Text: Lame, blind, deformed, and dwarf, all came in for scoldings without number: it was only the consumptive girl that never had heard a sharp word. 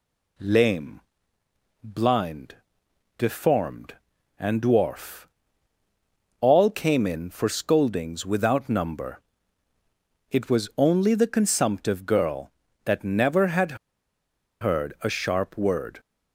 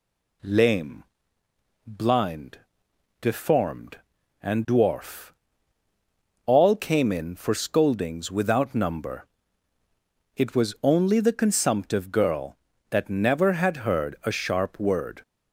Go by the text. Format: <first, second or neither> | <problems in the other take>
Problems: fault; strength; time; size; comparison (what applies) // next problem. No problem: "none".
second | pauses between "had" and "heard"; noticeable; at 13.7 s; 0.86 s long